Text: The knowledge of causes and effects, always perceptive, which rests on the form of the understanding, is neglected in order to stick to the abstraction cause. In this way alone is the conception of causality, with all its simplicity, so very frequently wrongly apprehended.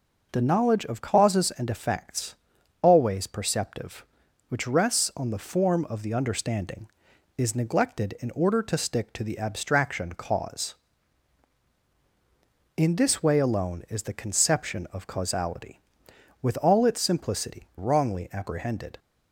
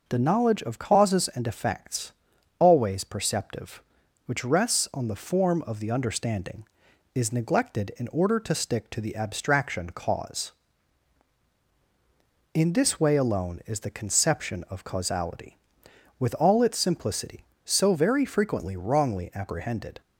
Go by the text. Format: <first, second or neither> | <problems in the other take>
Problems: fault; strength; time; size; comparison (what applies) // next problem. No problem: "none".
second | skips "so very frequently"; at 17.7 s